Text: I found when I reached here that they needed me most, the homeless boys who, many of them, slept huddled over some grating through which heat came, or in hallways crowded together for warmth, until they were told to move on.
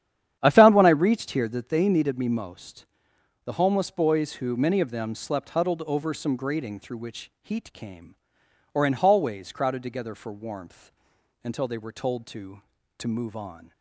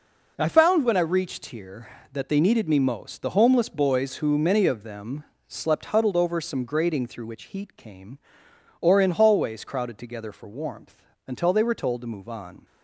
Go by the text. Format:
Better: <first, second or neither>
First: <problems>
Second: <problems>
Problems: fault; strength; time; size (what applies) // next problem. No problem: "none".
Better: second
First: starts louder than the rest; strong; until 1.4 s; 10 dB // says "to" twice; at 12.9 s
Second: none